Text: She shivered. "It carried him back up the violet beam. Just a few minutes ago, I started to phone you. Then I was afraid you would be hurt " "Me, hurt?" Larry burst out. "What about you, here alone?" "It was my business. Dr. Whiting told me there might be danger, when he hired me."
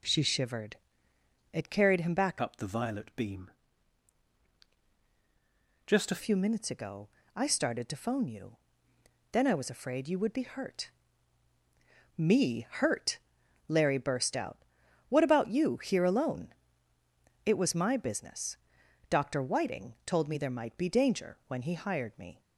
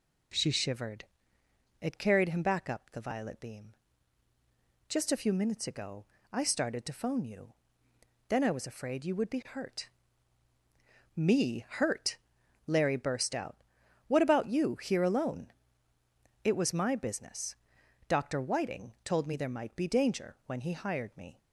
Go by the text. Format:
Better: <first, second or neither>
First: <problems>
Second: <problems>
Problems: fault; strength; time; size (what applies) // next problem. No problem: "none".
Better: second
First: changes voice from "up" to "a"; from 2.4 to 6.2 s; 3.8 s long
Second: none